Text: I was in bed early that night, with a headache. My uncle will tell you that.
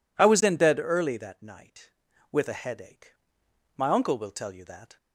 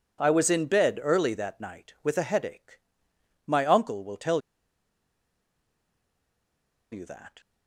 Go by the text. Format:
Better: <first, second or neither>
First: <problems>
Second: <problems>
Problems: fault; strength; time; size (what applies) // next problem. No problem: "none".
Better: first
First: none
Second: pauses between "tell" and "you"; strong; at 4.4 s; 2.5 s long